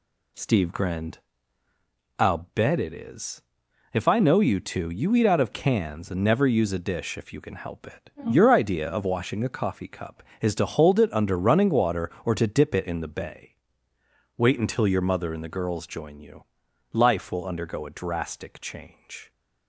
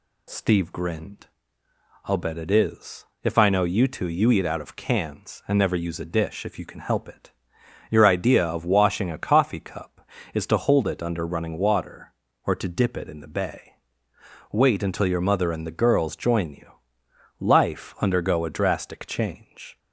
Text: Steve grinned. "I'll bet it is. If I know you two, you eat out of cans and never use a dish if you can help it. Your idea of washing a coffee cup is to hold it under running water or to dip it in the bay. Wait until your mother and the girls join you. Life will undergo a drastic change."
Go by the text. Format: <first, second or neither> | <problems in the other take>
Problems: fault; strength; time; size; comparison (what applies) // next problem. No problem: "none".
first | skips "will"; at 17.9 s